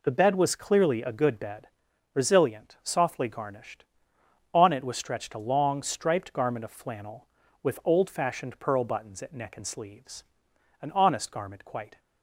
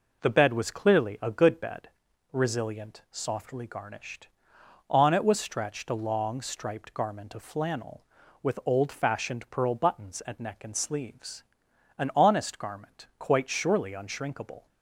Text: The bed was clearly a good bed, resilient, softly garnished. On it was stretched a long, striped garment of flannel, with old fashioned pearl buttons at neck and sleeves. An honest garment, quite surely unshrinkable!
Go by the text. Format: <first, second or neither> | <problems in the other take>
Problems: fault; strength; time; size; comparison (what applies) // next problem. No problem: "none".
second | stops before "surely unshrinkable"; at 11.9 s